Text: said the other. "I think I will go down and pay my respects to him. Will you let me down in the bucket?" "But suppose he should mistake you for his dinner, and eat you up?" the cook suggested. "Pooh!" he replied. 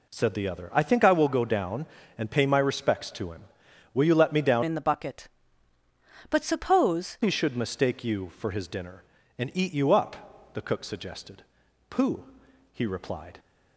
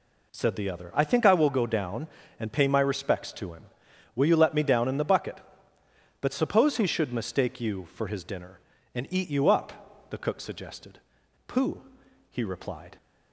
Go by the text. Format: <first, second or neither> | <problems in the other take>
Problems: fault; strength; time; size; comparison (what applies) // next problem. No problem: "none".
second | changes voice from "in" to "suppose"; from 4.6 to 7.1 s; 2.5 s long